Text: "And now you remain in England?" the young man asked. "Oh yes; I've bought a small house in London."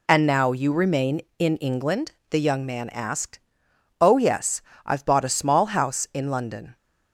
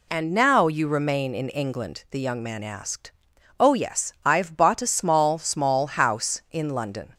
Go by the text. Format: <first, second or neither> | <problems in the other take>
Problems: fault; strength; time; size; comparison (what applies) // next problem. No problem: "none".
first | says "small" twice; at 5.3 s